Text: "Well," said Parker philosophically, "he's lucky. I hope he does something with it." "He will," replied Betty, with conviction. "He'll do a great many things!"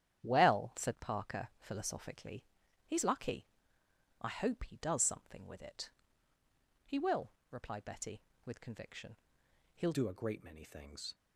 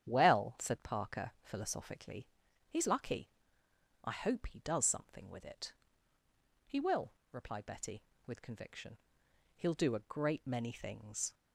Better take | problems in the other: second | starts louder than the rest; strong; until 1.2 s; 10 dB; strong in the second // changes voice at "do"; from 9.9 s on; 1.2 s long

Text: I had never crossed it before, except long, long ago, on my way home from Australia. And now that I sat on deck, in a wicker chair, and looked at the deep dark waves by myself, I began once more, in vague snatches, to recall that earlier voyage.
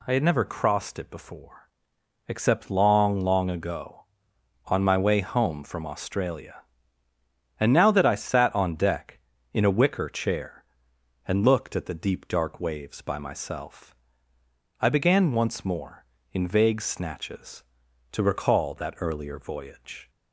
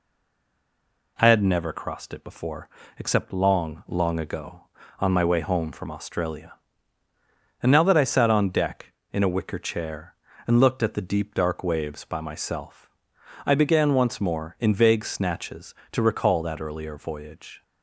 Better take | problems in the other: first | stays silent before the first word; until 1.1 s; 1.1 s long

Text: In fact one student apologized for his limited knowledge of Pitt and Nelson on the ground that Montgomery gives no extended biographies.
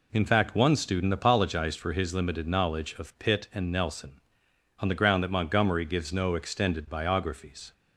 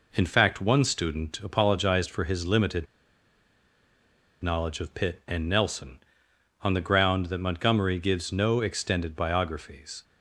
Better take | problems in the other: first | pauses between "limited" and "knowledge"; strong; at 2.8 s; 1.5 s long

